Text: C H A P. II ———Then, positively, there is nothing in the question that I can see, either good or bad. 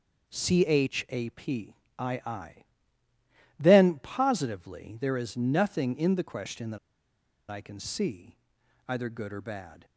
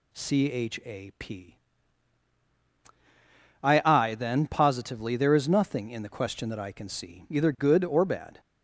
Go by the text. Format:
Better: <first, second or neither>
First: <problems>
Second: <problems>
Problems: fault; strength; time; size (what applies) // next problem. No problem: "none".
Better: second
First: pauses between "that" and "I"; noticeable; at 6.7 s; 0.72 s long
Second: none